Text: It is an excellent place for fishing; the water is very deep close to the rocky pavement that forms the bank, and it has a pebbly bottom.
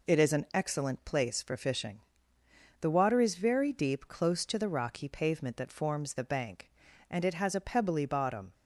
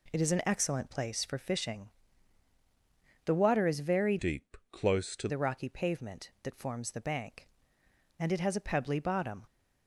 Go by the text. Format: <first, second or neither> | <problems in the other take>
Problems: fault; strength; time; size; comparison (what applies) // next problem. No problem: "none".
first | changes voice from "deep" to "to"; from 4.1 to 5.2 s; 1.1 s long